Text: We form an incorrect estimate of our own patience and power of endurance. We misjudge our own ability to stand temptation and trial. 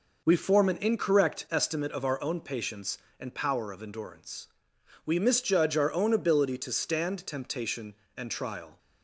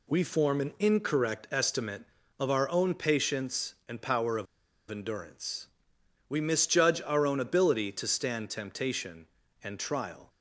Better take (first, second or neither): first